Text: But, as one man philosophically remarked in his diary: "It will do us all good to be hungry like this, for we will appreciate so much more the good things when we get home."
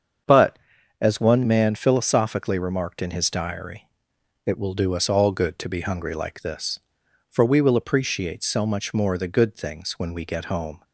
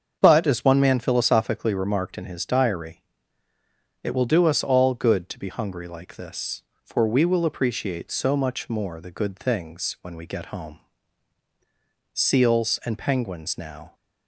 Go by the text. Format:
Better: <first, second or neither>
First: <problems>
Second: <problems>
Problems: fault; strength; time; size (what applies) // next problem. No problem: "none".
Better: first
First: starts louder than the rest; strong; until 1.6 s; 7 dB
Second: starts louder than the rest; until 1.2 s; 7 dB // goes on to say "Seals and penguins now"; strong; from 12.1 s on; 1.8 s long